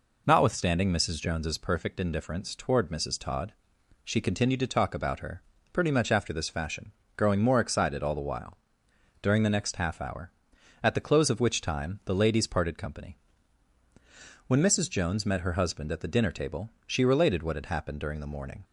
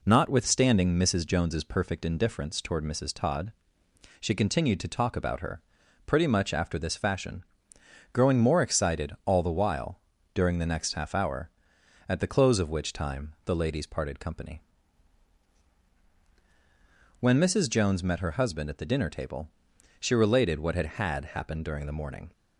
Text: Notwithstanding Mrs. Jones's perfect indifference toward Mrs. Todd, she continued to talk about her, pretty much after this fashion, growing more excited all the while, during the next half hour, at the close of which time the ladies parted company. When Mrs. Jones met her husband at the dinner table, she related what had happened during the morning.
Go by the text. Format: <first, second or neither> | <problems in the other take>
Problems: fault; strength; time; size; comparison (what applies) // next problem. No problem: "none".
first | says "had" twice; at 20.9 s